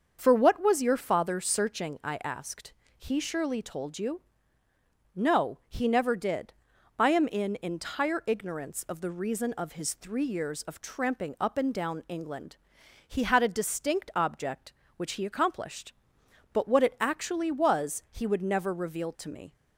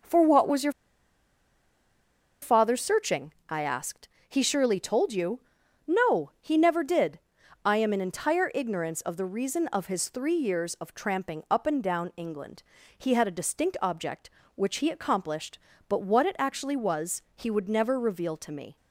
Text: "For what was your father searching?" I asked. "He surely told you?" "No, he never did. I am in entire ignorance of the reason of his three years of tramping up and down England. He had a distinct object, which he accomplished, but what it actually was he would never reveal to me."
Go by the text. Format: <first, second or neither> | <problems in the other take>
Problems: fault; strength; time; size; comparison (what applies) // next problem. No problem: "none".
first | starts louder than the rest; noticeable; until 2.7 s; 6 dB; also in the first // pauses between "your" and "father"; strong; at 0.7 s; 1.6 s long